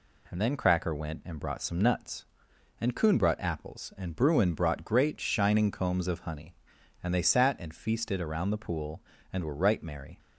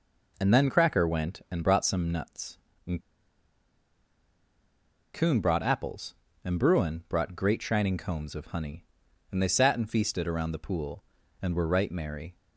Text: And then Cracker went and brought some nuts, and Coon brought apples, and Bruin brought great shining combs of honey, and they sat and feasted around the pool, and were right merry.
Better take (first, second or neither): first